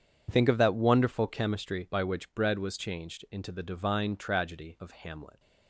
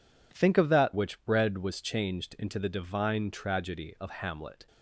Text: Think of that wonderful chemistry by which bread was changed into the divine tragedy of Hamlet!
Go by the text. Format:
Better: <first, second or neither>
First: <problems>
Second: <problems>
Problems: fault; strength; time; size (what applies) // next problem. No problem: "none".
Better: first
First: none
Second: skips "wonderful chemistry by"; at 0.9 s